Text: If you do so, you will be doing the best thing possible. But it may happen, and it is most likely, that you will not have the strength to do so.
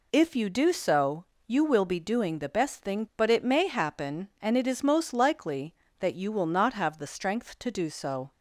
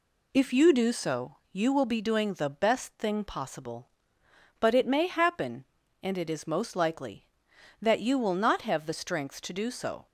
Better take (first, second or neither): second